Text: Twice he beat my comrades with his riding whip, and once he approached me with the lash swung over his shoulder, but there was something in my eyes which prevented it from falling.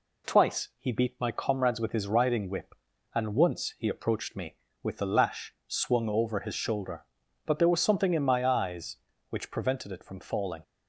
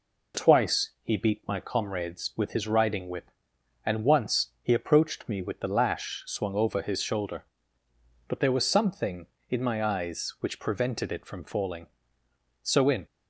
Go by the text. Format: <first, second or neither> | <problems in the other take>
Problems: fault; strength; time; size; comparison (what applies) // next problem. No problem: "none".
first | goes on to say "So in"; slight; from 12.6 s on; 0.44 s long